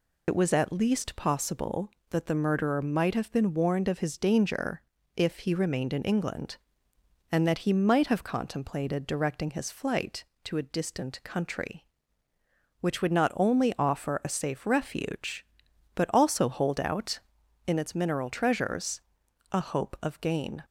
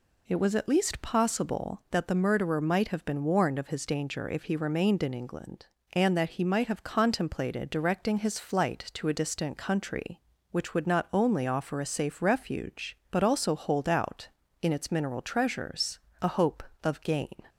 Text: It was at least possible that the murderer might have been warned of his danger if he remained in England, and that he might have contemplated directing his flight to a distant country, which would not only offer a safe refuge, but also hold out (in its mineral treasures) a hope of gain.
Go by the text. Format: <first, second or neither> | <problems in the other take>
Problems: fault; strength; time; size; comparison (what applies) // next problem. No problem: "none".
second | loses the start of "It"; at 0.2 s; 60 ms // pauses between "danger" and "if"; slight; at 4.8 s; 0.34 s long